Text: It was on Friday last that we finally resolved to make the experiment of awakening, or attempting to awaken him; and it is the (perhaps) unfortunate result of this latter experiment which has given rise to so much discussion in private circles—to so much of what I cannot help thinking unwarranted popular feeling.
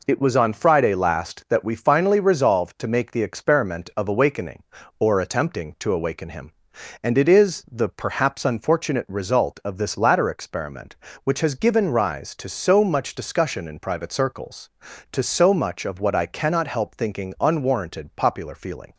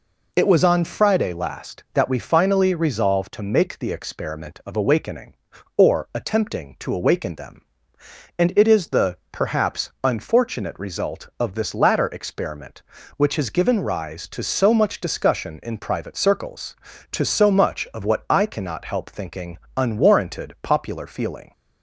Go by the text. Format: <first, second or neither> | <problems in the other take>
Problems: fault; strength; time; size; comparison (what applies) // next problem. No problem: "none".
first | says "them" for "him"; at 7.3 s // pauses between "thinking" and "unwarranted"; slight; at 19.5 s; 0.18 s long